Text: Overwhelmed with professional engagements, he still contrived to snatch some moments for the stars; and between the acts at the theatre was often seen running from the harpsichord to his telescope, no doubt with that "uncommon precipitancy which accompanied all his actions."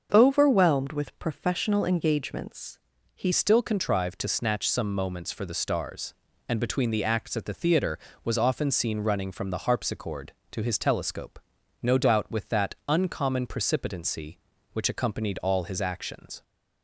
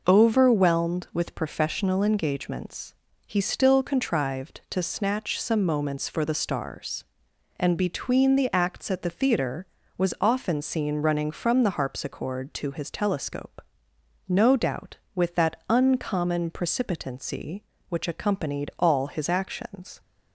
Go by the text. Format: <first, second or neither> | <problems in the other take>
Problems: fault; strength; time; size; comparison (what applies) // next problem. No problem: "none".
second | starts louder than the rest; until 1.1 s; 6.5 dB // changes voice at "still"; from 3.3 s on; 13.1 s long